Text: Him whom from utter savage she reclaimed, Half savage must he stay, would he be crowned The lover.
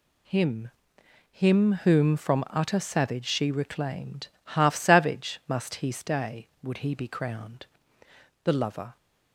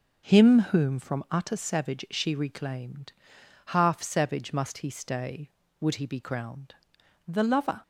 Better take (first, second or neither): second